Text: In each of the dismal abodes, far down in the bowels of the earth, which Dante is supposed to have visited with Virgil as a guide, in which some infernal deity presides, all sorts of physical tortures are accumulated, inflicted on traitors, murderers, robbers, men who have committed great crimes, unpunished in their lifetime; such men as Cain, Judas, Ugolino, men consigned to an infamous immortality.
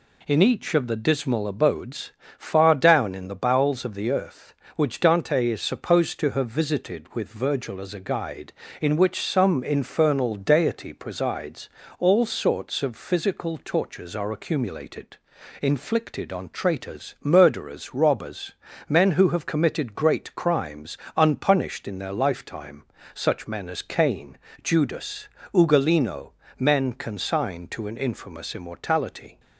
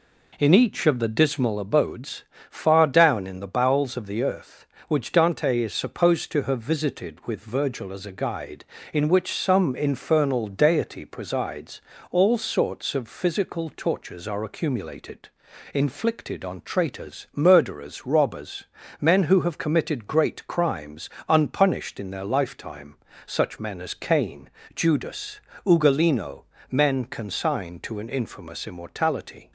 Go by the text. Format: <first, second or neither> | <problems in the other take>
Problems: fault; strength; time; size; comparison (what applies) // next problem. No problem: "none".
first | starts louder than the rest; until 1.6 s; 3.5 dB